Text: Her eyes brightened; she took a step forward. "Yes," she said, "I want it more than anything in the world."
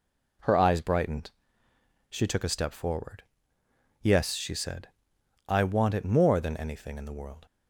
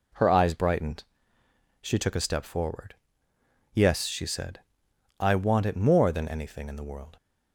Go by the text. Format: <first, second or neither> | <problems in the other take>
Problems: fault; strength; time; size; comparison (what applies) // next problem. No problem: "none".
neither | none